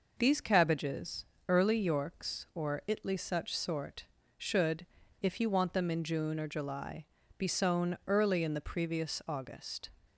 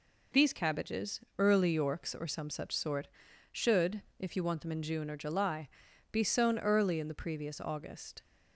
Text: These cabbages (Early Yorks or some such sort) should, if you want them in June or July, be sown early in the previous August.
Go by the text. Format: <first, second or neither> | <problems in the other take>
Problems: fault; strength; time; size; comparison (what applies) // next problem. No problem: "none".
second | says "itly" for "some"; at 2.8 s